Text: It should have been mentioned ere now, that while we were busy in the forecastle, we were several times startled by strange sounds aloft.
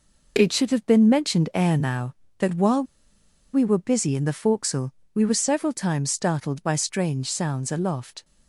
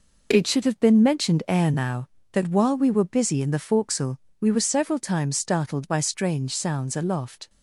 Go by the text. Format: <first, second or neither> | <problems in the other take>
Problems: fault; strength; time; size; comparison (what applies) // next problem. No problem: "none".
second | pauses between "while" and "we"; noticeable; at 2.8 s; 0.70 s long